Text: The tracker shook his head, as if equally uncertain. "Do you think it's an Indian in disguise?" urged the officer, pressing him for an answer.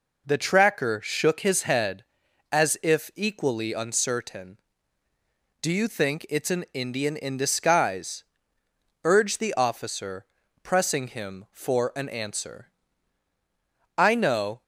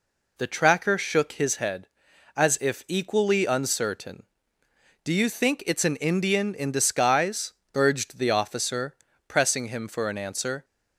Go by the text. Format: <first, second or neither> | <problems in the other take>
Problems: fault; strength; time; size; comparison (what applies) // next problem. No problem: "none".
second | goes on to say "I know"; noticeable; from 13.9 s on; 0.64 s long